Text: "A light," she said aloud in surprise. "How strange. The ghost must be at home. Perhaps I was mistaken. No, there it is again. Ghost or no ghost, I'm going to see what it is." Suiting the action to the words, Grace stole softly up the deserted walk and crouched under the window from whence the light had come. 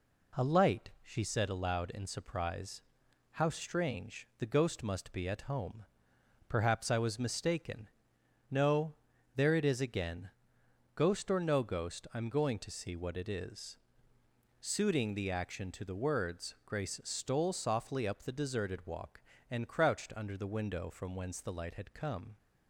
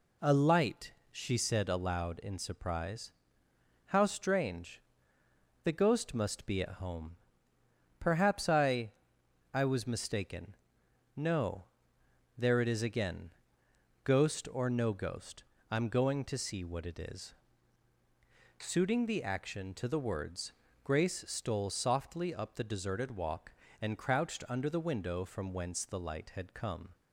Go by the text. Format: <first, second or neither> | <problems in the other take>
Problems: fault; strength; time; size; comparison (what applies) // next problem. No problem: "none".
first | says "I" twice; at 9.5 s